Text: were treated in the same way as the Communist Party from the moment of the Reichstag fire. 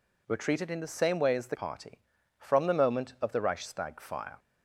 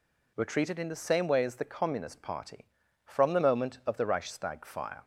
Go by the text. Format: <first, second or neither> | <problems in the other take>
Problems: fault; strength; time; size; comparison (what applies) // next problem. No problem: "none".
second | skips "Communist"; at 1.5 s